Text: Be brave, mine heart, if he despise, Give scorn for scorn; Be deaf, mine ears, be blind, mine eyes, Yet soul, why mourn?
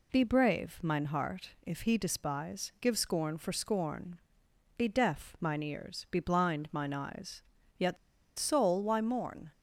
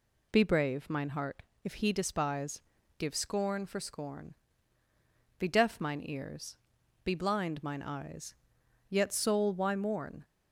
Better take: second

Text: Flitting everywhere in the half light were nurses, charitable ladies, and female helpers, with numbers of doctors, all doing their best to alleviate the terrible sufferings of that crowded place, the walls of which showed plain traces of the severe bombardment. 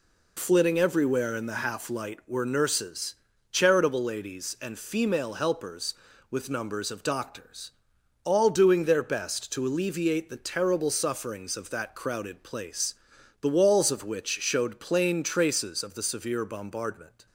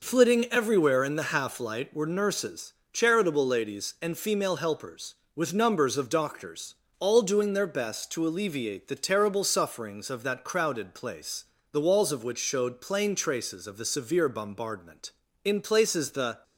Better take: first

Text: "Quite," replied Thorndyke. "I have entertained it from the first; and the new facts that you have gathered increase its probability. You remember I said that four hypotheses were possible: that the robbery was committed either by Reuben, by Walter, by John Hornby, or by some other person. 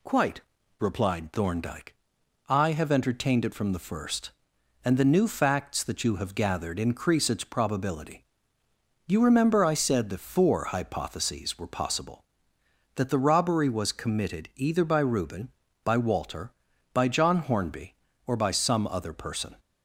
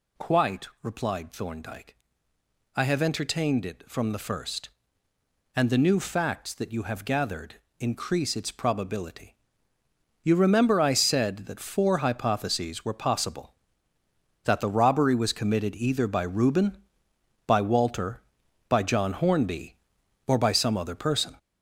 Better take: first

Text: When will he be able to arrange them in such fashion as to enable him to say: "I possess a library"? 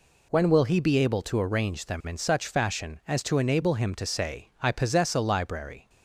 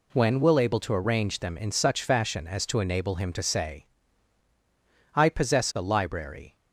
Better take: first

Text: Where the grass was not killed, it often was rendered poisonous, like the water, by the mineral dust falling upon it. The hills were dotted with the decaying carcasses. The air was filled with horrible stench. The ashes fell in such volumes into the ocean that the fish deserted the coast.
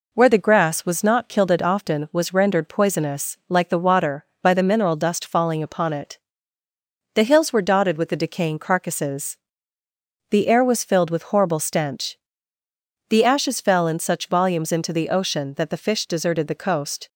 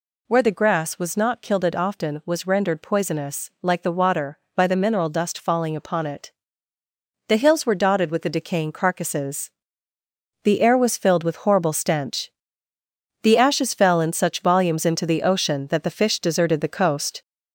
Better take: first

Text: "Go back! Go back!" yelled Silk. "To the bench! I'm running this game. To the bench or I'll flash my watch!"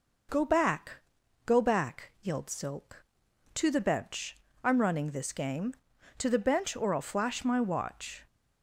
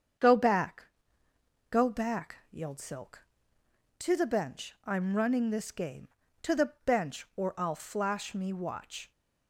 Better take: first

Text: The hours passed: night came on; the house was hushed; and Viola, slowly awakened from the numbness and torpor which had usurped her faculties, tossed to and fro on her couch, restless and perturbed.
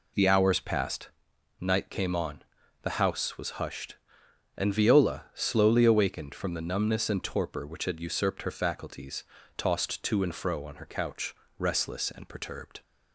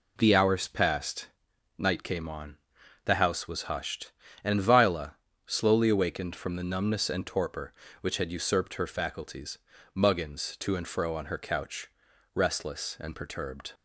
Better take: first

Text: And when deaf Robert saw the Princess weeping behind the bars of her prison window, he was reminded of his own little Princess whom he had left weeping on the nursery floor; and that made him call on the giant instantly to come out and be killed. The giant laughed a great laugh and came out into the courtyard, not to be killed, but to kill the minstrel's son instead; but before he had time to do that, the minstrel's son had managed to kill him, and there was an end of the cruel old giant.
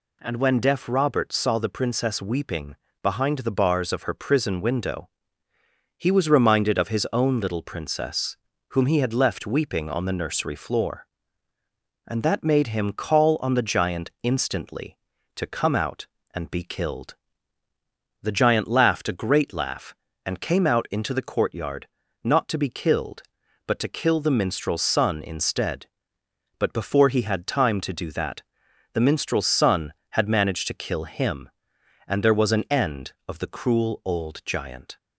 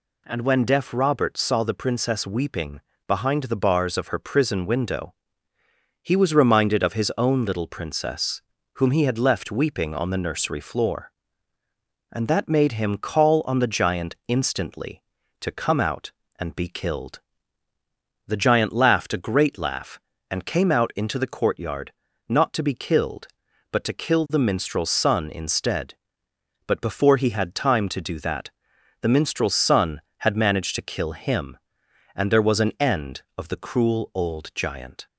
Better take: neither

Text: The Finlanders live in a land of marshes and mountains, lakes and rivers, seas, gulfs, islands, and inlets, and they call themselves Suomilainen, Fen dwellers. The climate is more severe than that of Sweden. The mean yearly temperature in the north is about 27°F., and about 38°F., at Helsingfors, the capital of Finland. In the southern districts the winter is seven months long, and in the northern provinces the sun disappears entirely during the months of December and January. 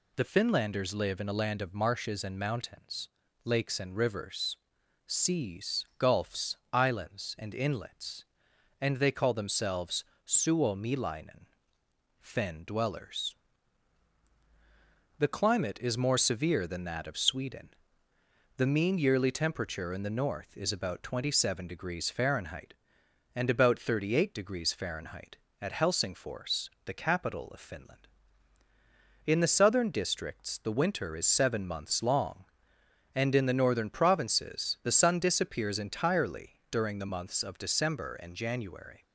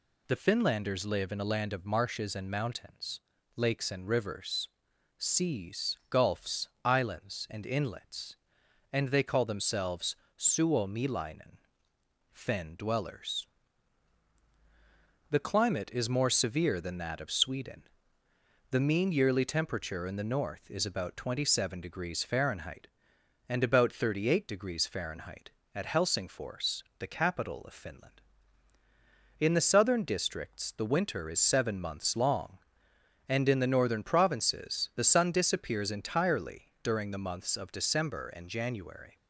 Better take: neither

